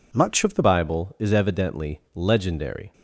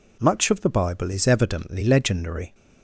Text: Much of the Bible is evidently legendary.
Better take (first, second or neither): second